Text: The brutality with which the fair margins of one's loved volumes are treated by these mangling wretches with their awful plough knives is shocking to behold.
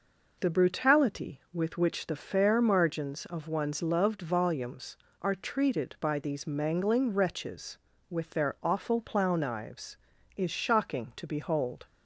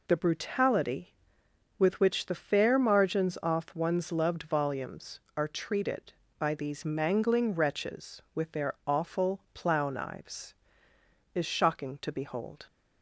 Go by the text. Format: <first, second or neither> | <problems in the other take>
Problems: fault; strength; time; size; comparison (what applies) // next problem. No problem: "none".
first | says "off" for "of"; at 3.4 s